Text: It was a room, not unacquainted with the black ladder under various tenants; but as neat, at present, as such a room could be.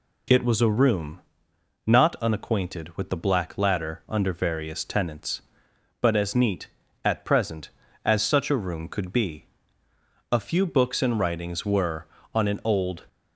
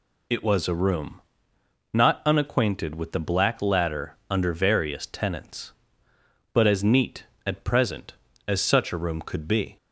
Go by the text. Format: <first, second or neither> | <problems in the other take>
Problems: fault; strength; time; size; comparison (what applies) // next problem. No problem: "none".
second | goes on to say "A few books and writings were on an old"; strong; from 10.3 s on; 2.7 s long